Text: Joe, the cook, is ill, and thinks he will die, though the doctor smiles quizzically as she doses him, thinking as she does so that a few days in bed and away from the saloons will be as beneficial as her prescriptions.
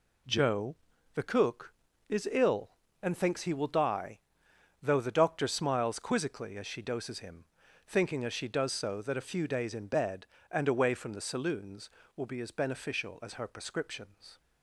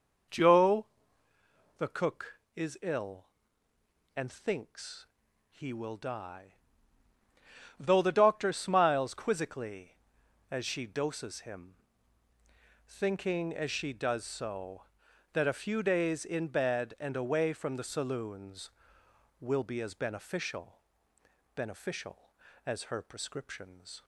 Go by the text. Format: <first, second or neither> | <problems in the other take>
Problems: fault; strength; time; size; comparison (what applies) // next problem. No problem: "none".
first | pauses between "thinks" and "he"; at 5.0 s; 0.44 s long // says "beneficial" twice; at 21.5 s